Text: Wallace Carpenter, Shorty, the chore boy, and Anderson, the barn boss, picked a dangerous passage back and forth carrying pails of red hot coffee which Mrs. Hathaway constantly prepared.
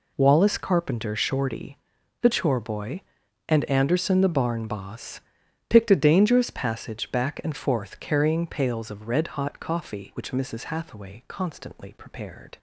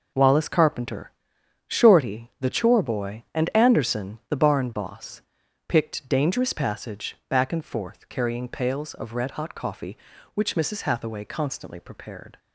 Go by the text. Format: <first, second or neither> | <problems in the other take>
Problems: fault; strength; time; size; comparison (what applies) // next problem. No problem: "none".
first | skips "a"; at 6.0 s